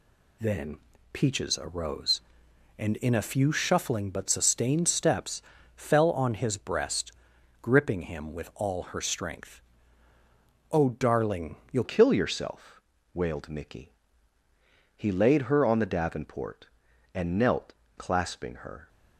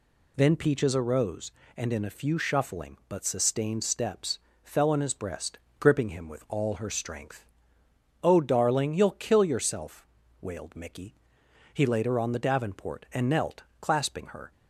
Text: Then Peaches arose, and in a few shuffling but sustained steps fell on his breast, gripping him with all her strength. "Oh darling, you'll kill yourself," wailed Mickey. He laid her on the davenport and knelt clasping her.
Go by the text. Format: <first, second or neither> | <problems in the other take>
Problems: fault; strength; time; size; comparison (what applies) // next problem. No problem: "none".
second | pauses between "Then" and "Peaches"; slight; at 0.7 s; 0.34 s long // pauses between "steps" and "fell"; slight; at 5.4 s; 0.34 s long; slight in the second // changes voice at "kill"; from 11.8 s on; 7.0 s long // pauses between "knelt" and "clasping"; slight; at 17.7 s; 0.24 s long; slight in the second